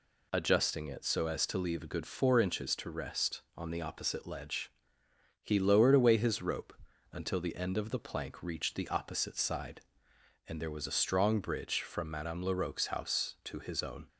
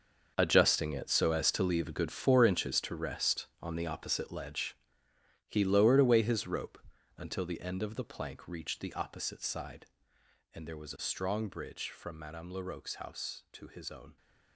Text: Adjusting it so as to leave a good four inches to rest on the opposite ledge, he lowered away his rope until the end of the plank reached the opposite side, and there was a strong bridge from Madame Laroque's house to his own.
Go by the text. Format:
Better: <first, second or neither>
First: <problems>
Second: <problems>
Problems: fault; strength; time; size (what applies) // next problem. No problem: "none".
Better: first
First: pauses between "rope" and "until"; at 6.7 s; 0.40 s long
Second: gets quieter; strong; throughout; 13.5 dB // pauses between "rope" and "until"; at 6.7 s; 0.40 s long